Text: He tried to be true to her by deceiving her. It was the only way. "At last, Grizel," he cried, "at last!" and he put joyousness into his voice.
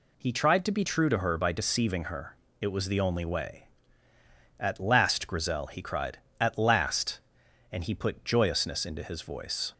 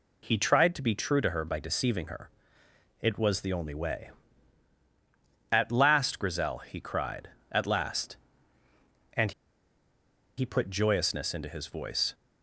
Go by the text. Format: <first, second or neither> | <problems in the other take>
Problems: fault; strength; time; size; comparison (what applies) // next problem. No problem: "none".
first | pauses between "and" and "he"; at 9.3 s; 1.0 s long